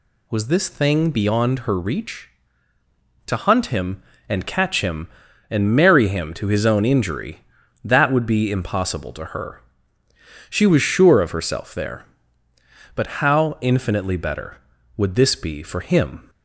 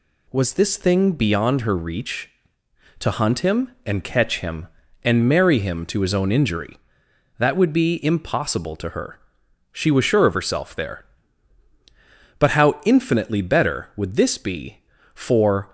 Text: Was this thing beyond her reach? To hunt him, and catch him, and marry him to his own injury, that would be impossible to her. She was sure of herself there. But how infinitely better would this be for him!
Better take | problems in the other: first | stops before "him"; at 15.6 s

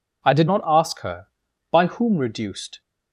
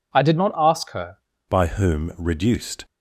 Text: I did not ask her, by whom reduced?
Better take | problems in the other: first | changes voice at "by"; from 1.4 s on; 1.4 s long

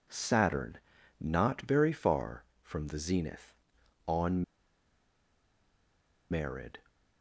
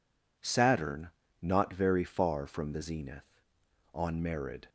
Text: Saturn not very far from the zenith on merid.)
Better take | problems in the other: second | pauses between "Saturn" and "not"; at 0.7 s; 0.42 s long; slight in the second // pauses between "on" and "merid"; strong; at 4.4 s; 1.8 s long

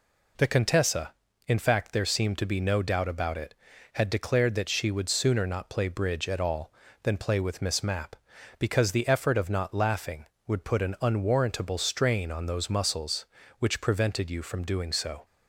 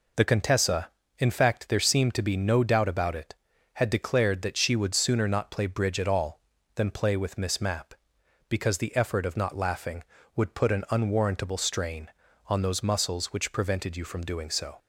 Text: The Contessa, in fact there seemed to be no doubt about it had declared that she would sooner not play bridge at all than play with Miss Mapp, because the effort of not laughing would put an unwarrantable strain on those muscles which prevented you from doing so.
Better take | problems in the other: neither | none

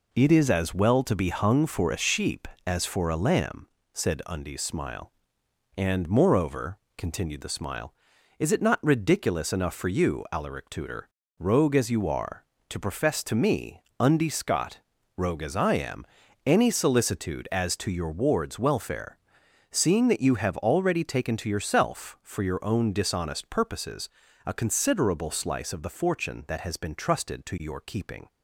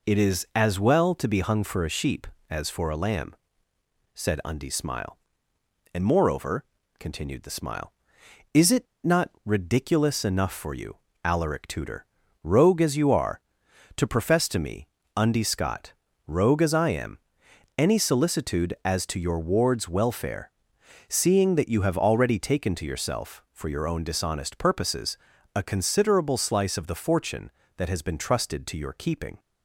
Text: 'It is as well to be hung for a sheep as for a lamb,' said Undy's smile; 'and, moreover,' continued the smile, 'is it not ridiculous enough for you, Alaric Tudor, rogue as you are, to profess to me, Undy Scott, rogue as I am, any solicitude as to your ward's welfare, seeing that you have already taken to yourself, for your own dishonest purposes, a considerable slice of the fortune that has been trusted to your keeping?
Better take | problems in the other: first | pauses between "it" and "not"; slight; at 8.8 s; 0.19 s long

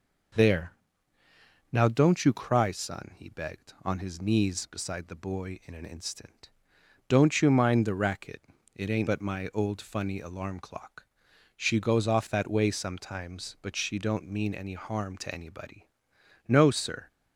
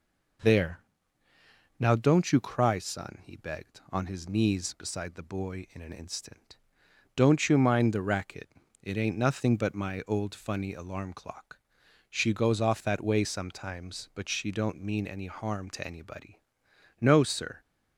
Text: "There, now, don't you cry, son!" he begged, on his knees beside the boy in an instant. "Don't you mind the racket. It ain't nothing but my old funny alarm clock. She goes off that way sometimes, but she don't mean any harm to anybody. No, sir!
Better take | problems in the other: second | skips "nothing"; at 9.0 s

